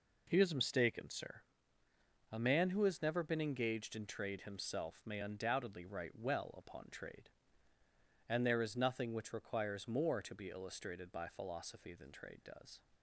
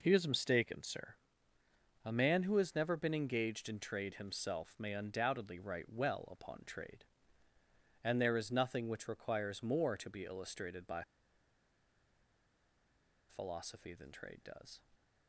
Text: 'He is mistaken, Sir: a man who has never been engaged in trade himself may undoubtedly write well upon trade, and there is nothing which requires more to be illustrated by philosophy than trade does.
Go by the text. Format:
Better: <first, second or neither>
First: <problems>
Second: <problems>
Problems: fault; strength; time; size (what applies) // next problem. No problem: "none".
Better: first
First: none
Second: pauses between "by" and "philosophy"; strong; at 11.0 s; 2.2 s long